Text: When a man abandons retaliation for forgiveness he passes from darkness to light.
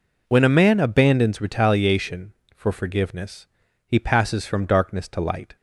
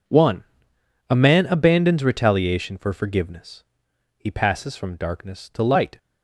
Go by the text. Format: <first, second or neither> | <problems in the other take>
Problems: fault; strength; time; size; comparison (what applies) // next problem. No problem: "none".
first | says "One" for "When"; at 0.0 s // pauses between "forgiveness" and "he"; noticeable; at 3.6 s; 0.52 s long; also in the first